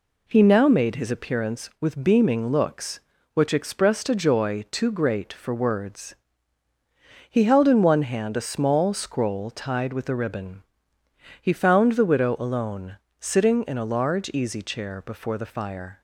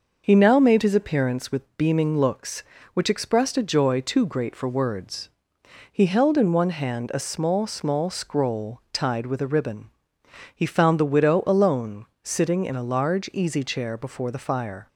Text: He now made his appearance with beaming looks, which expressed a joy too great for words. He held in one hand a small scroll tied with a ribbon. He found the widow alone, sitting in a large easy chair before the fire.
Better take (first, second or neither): first